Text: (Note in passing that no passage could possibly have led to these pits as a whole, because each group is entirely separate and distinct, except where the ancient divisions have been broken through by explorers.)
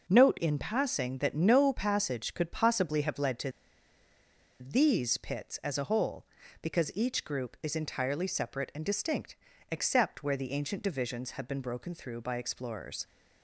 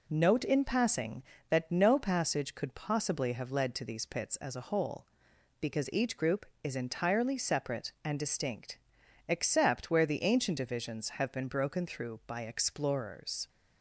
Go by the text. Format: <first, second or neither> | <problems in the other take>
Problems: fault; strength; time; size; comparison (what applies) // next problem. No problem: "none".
second | pauses between "to" and "these"; at 3.5 s; 1.0 s long